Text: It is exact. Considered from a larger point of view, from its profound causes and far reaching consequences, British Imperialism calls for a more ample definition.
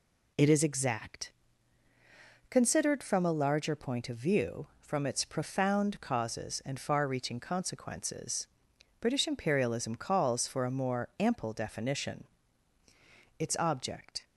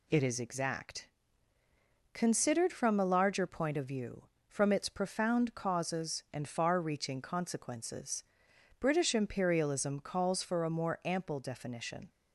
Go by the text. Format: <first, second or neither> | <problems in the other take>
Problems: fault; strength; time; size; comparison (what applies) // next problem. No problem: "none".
second | goes on to say "Its object"; noticeable; from 13.3 s on; 0.86 s long